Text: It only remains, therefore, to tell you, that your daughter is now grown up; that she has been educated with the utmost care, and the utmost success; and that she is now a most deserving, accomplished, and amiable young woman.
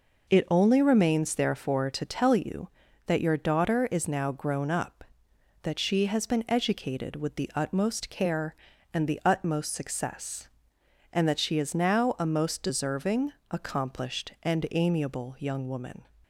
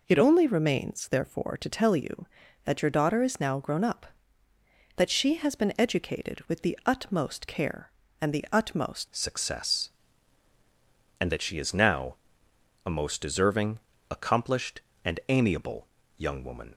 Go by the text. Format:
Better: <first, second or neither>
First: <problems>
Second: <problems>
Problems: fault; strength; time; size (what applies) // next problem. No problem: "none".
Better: first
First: none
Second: changes voice at "success"; from 9.1 s on; 7.6 s long // pauses between "now" and "a"; noticeable; at 12.1 s; 0.68 s long // pauses between "amiable" and "young"; slight; at 15.8 s; 0.30 s long